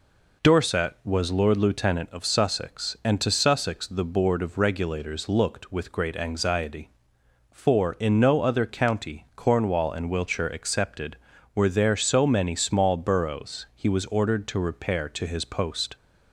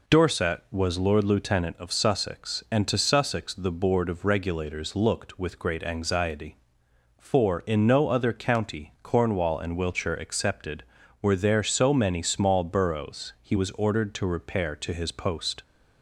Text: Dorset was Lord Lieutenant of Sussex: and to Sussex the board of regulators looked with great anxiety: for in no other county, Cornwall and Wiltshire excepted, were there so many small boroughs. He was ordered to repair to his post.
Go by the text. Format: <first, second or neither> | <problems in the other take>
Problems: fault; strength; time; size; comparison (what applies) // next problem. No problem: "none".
neither | none